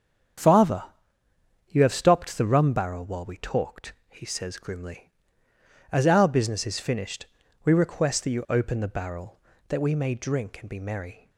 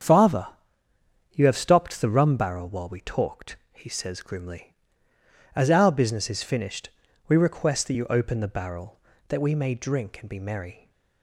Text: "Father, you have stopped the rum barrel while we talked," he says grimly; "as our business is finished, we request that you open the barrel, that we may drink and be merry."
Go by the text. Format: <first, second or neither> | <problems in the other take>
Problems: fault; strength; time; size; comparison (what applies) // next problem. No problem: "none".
neither | starts louder than the rest; strong; the same in both